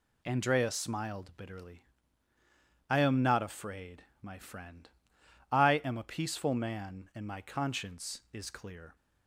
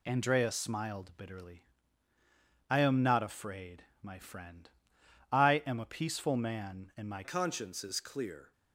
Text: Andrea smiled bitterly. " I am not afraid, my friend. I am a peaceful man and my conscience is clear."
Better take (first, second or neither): first